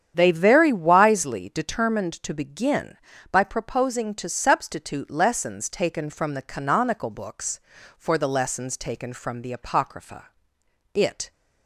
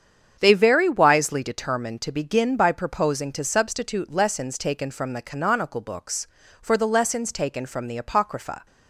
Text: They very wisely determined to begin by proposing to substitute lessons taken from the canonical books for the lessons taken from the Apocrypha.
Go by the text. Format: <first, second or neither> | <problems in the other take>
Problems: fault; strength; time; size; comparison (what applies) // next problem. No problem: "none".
second | starts louder than the rest; strong; until 1.1 s; 9 dB; strong in the second // goes on to say "It"; slight; from 10.9 s on; 0.38 s long